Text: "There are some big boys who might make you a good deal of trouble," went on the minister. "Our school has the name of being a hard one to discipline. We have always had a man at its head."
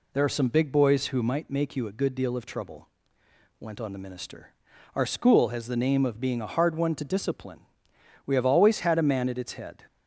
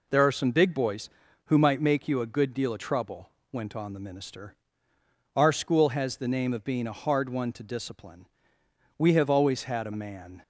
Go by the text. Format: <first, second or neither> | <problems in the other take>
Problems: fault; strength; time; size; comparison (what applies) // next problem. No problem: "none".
first | stops before "at its head"; at 10.4 s